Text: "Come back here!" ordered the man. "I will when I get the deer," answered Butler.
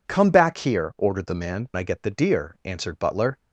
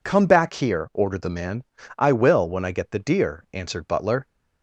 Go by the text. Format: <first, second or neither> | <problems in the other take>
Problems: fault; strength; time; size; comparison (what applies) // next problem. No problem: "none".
second | skips "I will when"; at 1.7 s